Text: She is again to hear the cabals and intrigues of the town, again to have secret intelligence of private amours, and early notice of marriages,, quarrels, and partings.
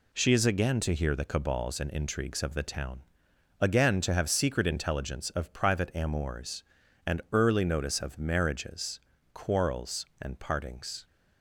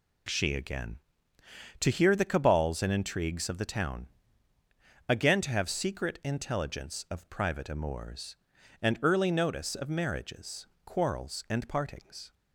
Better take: first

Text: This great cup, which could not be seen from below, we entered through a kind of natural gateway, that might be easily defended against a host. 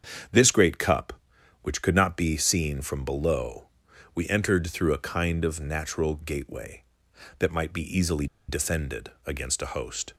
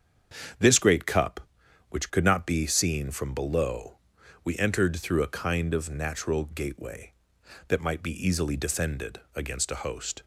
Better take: second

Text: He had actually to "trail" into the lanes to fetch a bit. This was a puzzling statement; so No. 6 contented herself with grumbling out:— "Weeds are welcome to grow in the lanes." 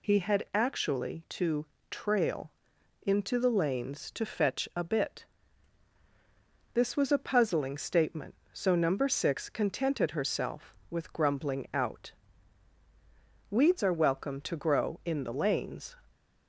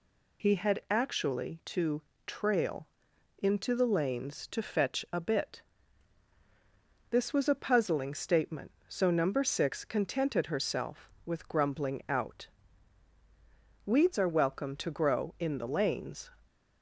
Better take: neither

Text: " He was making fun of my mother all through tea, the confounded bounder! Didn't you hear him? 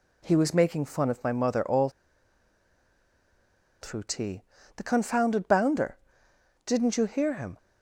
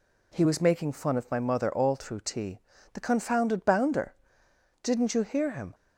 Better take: second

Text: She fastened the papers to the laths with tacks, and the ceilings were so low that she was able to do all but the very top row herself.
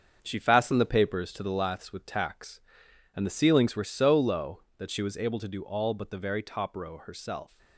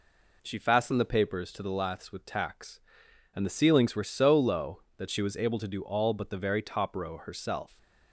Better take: second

